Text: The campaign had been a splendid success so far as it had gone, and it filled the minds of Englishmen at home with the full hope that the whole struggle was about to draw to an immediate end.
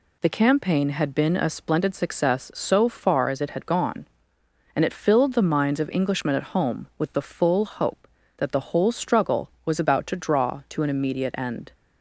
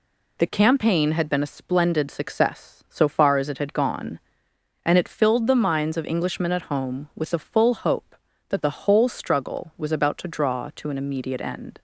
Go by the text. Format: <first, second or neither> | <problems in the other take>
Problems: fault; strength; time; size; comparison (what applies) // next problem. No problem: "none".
neither | none